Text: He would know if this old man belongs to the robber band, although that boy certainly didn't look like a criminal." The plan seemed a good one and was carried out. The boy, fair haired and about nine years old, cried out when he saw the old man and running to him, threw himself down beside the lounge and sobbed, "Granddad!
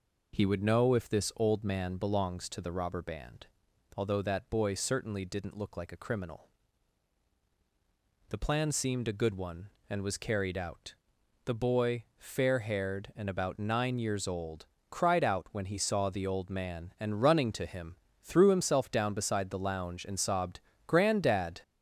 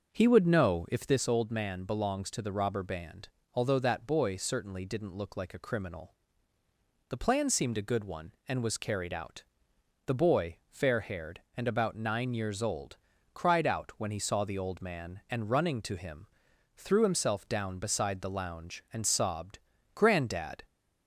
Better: first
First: none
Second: starts louder than the rest; until 1.3 s; 6.5 dB

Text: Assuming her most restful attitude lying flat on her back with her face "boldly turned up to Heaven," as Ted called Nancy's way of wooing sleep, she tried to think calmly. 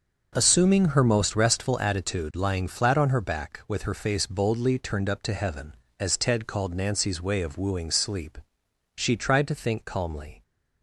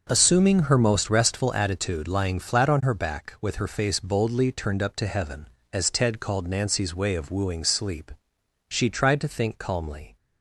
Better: neither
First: none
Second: none

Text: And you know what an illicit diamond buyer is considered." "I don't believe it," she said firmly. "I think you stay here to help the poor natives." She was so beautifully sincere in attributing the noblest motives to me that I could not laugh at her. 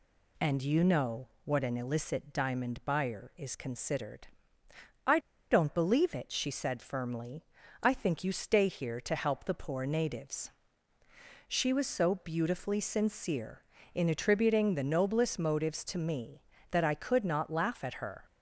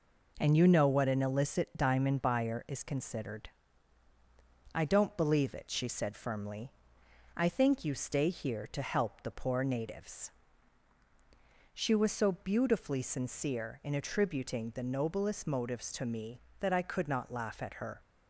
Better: second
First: pauses between "know" and "what"; slight; at 1.2 s; 0.16 s long // pauses between "I" and "don't"; slight; at 5.1 s; 0.32 s long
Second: none

